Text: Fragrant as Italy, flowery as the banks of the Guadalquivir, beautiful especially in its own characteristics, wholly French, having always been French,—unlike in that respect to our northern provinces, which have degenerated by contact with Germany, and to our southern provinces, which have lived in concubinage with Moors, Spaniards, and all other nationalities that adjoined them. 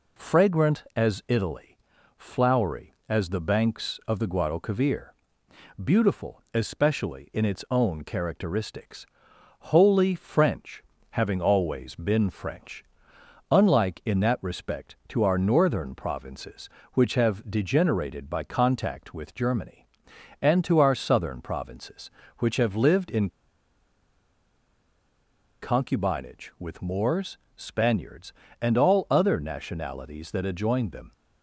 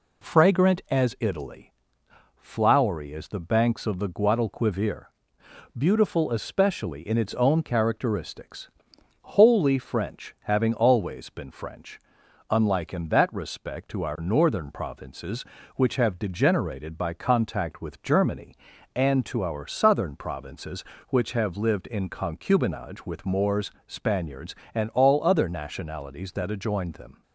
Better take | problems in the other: second | pauses between "in" and "concubinage"; strong; at 23.2 s; 2.3 s long

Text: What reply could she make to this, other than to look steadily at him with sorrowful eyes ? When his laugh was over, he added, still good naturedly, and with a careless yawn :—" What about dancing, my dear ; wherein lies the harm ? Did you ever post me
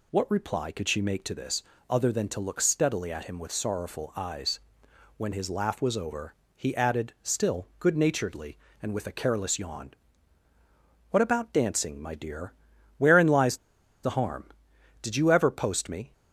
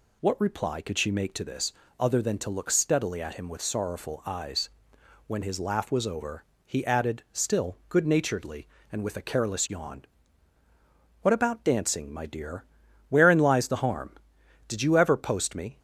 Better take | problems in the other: second | pauses between "lies" and "the"; noticeable; at 13.5 s; 0.46 s long

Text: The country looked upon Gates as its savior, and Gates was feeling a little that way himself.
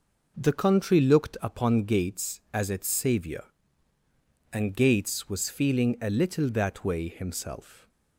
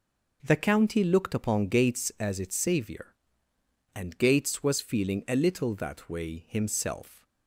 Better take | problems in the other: first | says "county" for "country"; at 0.5 s

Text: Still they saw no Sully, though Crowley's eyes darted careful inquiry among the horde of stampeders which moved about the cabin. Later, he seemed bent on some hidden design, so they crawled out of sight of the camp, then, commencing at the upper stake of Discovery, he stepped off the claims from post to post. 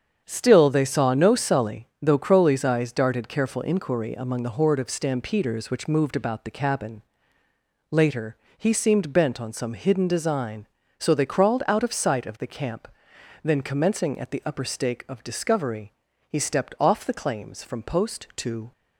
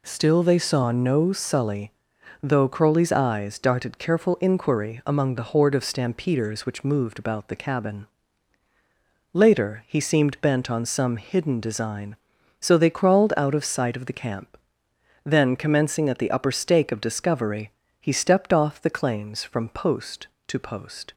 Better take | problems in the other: second | starts louder than the rest; strong; until 1.2 s; 7.5 dB // stops before "post"; at 18.7 s

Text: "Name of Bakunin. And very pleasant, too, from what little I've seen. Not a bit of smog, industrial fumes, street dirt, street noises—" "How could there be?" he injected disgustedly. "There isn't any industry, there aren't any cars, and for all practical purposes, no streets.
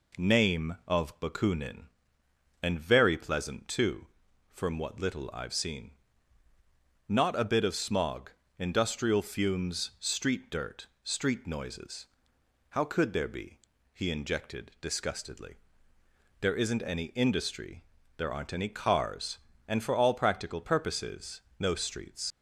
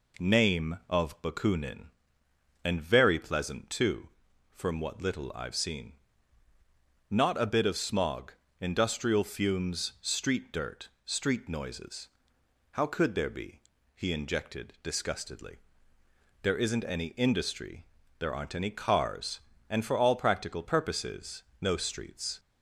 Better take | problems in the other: second | leaves "streets" unfinished; at 22.3 s; 70 ms

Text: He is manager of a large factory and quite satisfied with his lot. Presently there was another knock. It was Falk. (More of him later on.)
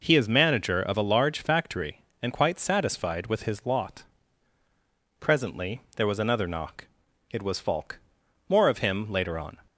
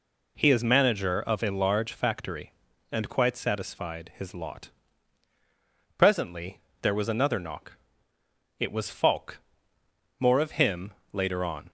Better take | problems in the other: first | skips "with"; at 4.1 s // pauses between "Presently" and "there"; slight; at 6.6 s; 0.22 s long // pauses between "him" and "later"; slight; at 10.9 s; 0.18 s long

